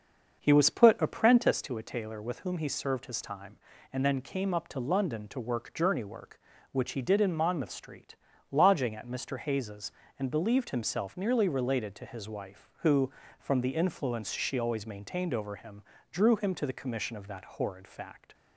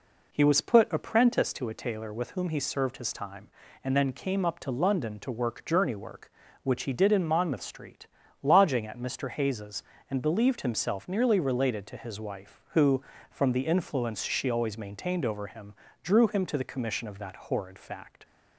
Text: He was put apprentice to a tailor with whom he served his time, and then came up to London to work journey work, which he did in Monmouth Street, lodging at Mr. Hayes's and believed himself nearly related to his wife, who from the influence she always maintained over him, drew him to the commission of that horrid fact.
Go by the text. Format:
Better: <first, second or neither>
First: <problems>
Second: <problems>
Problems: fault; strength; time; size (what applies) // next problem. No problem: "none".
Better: second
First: starts louder than the rest; until 1.7 s; 6.5 dB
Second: none